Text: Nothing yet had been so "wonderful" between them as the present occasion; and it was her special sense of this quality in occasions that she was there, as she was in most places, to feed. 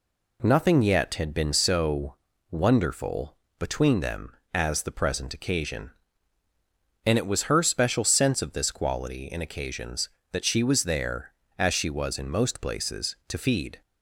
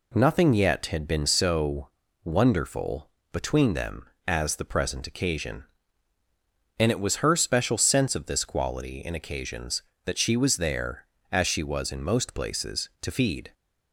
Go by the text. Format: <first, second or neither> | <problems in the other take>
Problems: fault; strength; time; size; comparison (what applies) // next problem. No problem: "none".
neither | pauses between "so" and "wonderful"; slight; the same in both // pauses between "wonderful" and "between"; slight; the same in both